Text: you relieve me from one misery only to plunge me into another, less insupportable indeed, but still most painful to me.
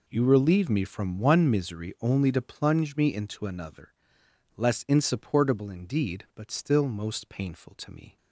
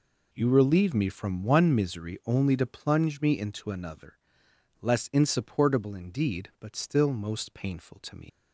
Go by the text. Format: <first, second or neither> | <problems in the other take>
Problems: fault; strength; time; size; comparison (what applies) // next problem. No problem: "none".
first | leaves "me" unfinished; at 8.2 s; 115 ms